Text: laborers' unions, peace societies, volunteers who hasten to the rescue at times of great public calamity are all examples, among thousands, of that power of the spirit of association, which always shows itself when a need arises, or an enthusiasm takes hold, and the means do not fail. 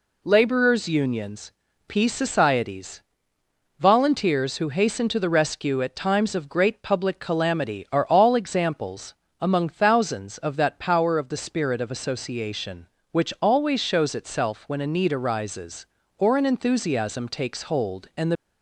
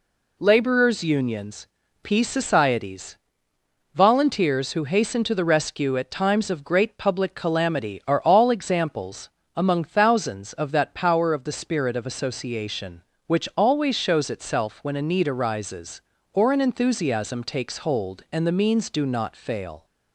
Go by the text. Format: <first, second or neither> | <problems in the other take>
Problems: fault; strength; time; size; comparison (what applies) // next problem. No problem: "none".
second | stops before "means do not fail"; at 18.3 s